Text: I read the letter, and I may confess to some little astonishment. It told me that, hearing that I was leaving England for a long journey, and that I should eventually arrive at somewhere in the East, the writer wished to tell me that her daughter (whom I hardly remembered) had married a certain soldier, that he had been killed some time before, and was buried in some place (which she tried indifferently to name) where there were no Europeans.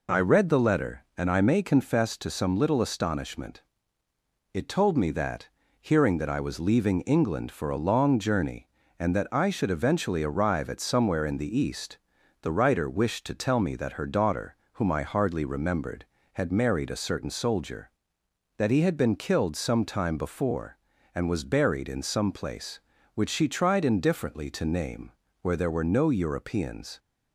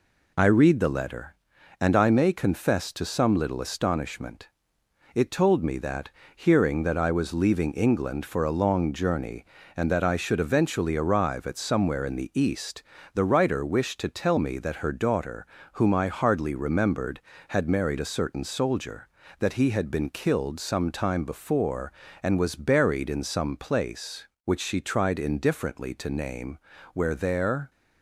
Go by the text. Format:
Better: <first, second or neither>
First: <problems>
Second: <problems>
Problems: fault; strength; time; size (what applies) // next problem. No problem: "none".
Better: first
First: none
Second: stops before "were no Europeans"; at 27.6 s